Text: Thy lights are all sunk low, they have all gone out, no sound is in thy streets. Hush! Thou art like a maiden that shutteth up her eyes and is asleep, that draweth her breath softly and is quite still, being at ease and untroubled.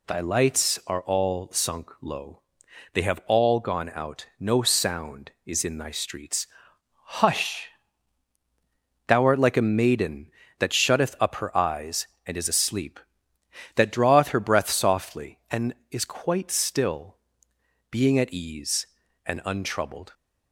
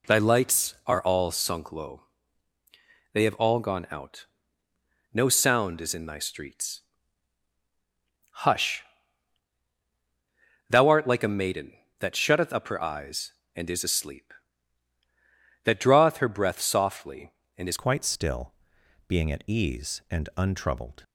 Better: first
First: none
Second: changes voice at "quite"; from 17.7 s on; 3.3 s long

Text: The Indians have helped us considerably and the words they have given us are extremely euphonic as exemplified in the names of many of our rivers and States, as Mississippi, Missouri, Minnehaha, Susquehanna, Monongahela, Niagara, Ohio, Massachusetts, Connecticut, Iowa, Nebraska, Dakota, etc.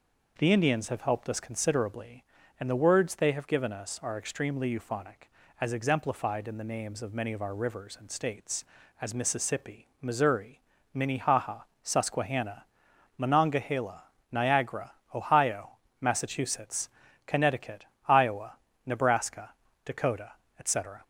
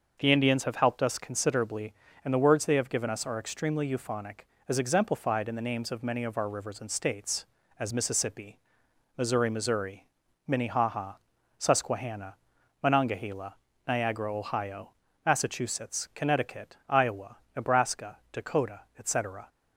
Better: first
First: none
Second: starts louder than the rest; until 1.2 s; 6 dB // says "Missouri" twice; at 9.5 s

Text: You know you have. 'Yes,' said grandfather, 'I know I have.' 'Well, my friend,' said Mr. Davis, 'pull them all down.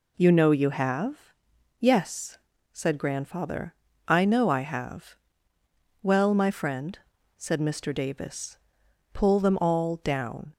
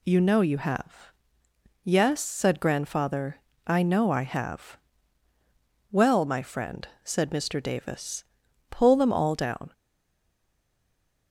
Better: first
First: none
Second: stays silent after the last word; noticeable; from 9.7 s on; 1.6 s long

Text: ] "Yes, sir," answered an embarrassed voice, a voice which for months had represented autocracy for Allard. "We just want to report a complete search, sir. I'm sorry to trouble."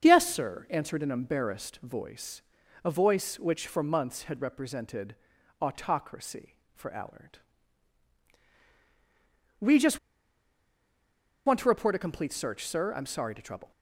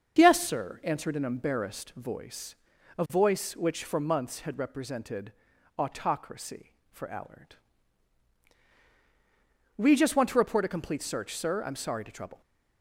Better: second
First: starts louder than the rest; until 1.0 s; 6.5 dB // pauses between "represented" and "autocracy"; noticeable; at 5.1 s; 0.46 s long // pauses between "just" and "want"; strong; at 9.9 s; 1.4 s long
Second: starts louder than the rest; until 1.2 s; 6.5 dB // pauses between "represented" and "autocracy"; noticeable; at 5.3 s; 0.46 s long

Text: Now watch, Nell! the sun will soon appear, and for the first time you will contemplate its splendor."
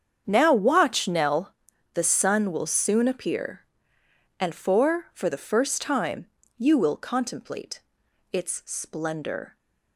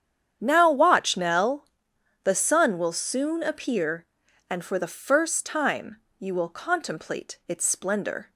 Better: second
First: starts louder than the rest; strong; until 1.2 s; 7.5 dB // says "for" twice; at 5.1 s // pauses between "time" and "you"; slight; at 6.2 s; 0.28 s long // pauses between "contemplate" and "its"; noticeable; at 7.8 s; 0.50 s long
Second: starts louder than the rest; strong; until 1.4 s; 9 dB // pauses between "time" and "you"; slight; at 6.0 s; 0.18 s long

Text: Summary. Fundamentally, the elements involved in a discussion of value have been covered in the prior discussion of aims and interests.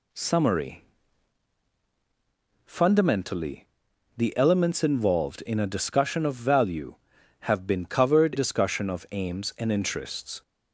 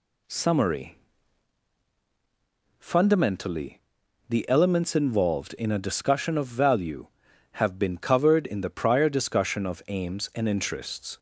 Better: second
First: skips "in the prior"; at 8.3 s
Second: none

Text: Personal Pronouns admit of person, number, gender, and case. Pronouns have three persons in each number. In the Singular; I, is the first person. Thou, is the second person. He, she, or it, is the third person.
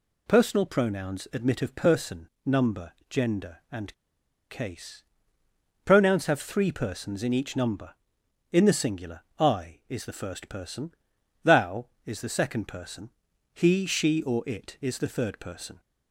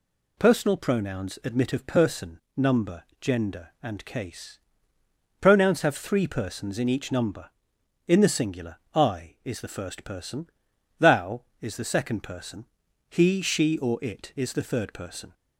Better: second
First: pauses between "and" and "case"; noticeable; at 3.9 s; 0.58 s long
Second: none

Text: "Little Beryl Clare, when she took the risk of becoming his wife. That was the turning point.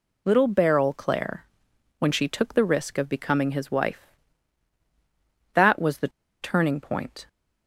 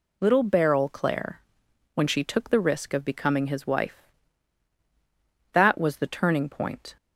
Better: second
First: pauses between "the" and "turning"; slight; at 6.0 s; 0.32 s long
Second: none

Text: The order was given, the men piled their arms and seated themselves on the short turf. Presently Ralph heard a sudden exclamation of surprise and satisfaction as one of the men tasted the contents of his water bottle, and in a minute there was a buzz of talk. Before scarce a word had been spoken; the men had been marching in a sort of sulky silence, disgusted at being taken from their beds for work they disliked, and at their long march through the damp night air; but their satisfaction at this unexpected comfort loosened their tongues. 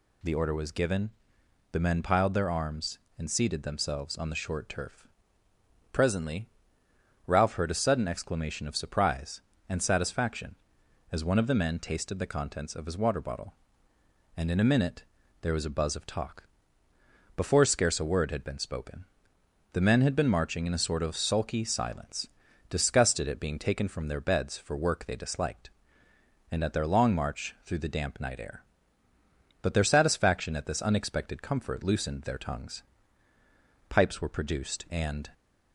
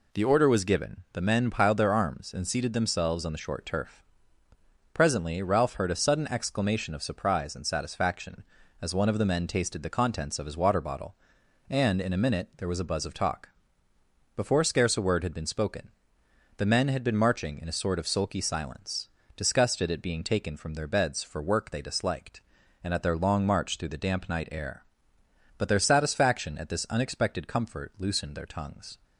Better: second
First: pauses between "Presently" and "Ralph"; noticeable; at 6.4 s; 0.78 s long // pauses between "minute" and "there"; at 15.0 s; 0.38 s long // goes on to say "Pipes were produced and"; from 33.8 s on; 1.4 s long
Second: none

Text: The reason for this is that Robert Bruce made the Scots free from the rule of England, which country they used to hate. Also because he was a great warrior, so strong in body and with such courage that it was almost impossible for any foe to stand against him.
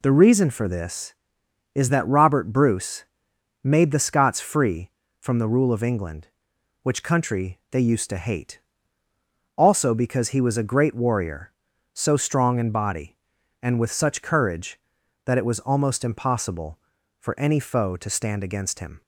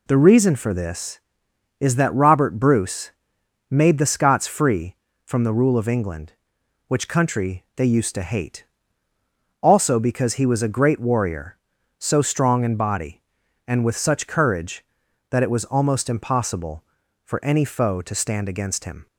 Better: neither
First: pauses between "Bruce" and "made"; noticeable; at 3.0 s; 0.58 s long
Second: pauses between "Bruce" and "made"; noticeable; at 3.1 s; 0.58 s long

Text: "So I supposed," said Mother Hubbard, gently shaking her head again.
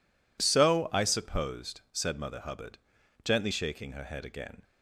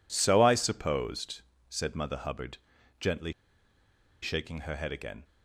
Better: first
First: none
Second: pauses between "gently" and "shaking"; noticeable; at 3.3 s; 0.91 s long

